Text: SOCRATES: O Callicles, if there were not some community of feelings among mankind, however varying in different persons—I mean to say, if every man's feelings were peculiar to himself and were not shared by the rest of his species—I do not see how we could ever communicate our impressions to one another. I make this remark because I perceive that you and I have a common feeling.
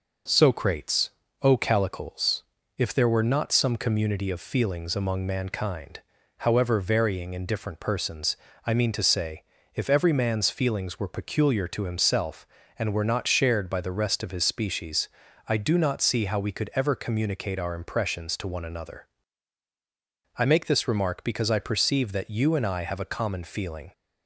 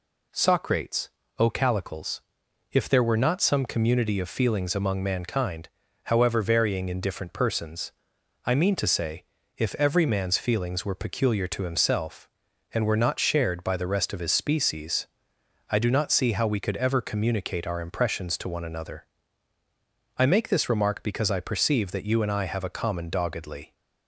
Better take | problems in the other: first | says "doggedly" for "feeling"; at 23.0 s

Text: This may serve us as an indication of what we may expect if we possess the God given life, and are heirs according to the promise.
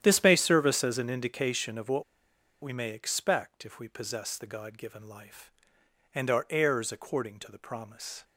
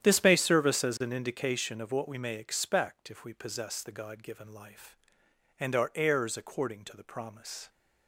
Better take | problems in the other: second | starts louder than the rest; strong; until 1.0 s; 10 dB; strong in the second // pauses between "what" and "we"; noticeable; at 2.0 s; 0.60 s long

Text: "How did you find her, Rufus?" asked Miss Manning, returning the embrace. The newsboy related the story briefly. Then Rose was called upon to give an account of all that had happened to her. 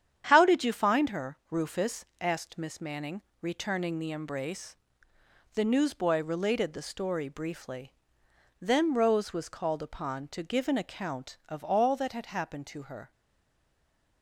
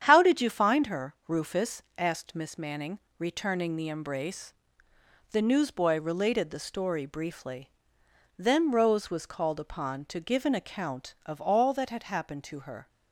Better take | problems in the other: second | starts louder than the rest; strong; until 1.3 s; 9 dB; strong in the second // stays silent after the last word; from 13.1 s on; 1.1 s long

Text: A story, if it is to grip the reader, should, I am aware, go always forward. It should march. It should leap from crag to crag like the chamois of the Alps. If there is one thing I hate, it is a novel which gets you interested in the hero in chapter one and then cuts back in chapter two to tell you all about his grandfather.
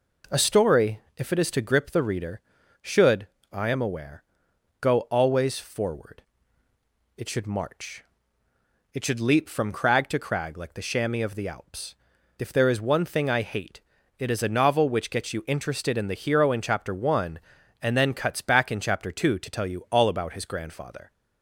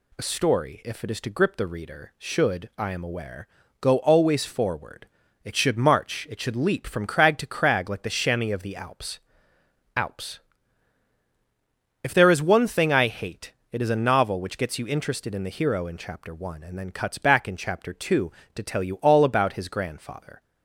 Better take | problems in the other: first | says "Alps" twice; at 9.9 s

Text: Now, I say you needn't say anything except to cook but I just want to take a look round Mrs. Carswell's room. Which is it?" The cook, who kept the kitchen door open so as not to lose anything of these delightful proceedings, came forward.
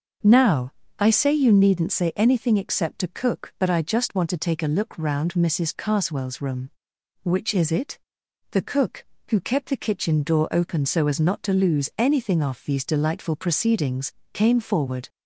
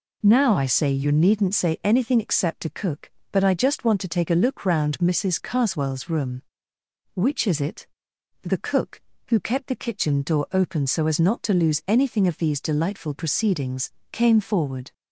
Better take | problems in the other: second | starts louder than the rest; noticeable; until 1.4 s; 6 dB // says "off" for "of"; at 12.4 s

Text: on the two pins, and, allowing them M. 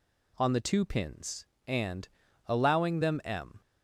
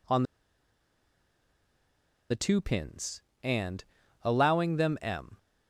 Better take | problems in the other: first | pauses between "on" and "the"; strong; at 0.2 s; 2.0 s long

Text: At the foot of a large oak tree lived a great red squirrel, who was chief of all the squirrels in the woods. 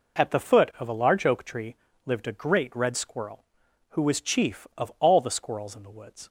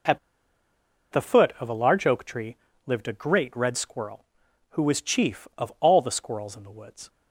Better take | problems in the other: first | pauses between "At" and "the"; noticeable; at 0.1 s; 0.93 s long // pauses between "tree" and "lived"; slight; at 2.5 s; 0.28 s long; slight in the first

